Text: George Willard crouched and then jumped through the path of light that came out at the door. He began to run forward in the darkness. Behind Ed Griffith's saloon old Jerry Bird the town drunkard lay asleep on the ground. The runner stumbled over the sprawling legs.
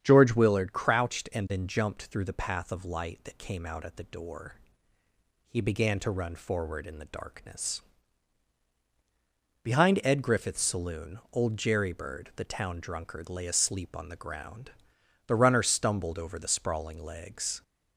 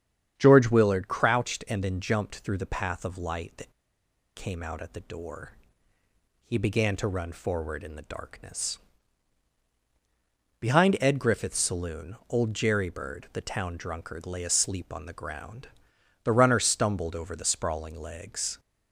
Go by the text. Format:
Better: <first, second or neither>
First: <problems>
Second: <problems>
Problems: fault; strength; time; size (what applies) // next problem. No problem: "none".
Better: first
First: starts louder than the rest; strong; until 1.0 s; 8.5 dB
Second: starts louder than the rest; strong; until 1.3 s; 8.5 dB // pauses between "that" and "came"; noticeable; at 3.7 s; 0.64 s long